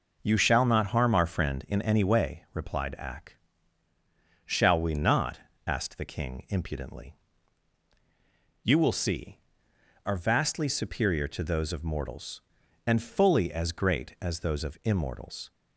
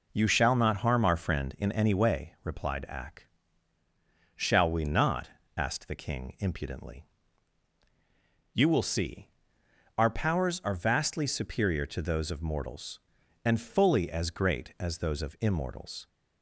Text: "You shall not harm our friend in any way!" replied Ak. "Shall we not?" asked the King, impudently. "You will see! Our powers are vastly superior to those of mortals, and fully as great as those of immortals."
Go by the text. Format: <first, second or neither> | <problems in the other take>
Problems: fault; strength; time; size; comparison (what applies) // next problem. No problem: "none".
second | skips "Our powers"; at 9.7 s